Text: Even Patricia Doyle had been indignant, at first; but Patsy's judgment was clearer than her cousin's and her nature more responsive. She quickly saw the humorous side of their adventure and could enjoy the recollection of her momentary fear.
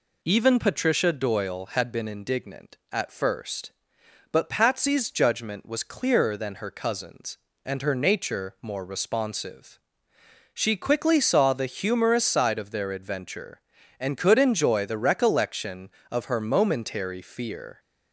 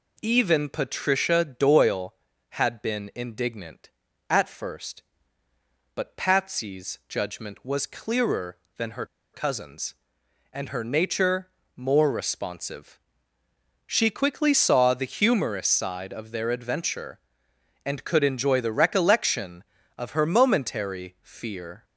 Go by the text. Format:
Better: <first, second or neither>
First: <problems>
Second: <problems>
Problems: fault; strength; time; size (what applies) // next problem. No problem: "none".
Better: first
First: none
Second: pauses between "her" and "cousin's"; slight; at 9.0 s; 0.27 s long // pauses between "nature" and "more"; slight; at 11.4 s; 0.28 s long